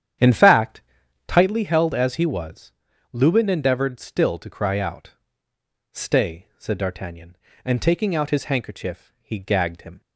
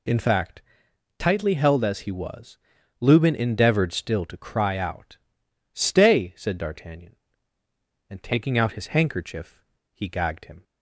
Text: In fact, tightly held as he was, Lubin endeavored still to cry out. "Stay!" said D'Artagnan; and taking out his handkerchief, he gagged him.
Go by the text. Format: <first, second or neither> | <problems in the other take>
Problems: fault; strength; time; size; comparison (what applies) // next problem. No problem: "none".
second | starts louder than the rest; strong; until 1.7 s; 9.5 dB